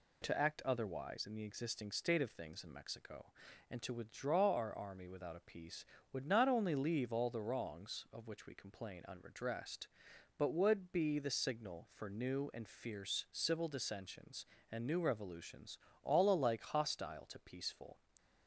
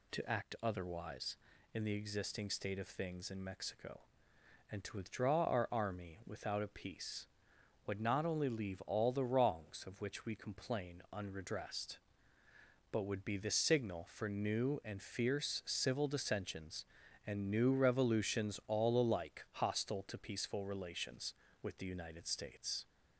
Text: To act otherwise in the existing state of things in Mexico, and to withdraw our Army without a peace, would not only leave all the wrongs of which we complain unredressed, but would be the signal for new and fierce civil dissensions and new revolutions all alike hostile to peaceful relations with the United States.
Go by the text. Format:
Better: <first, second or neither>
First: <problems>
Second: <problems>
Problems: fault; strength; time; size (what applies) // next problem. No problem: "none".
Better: second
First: pauses between "revolutions" and "all"; slight; at 15.7 s; 0.28 s long // stops before "relations with the United States"; at 18.1 s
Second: none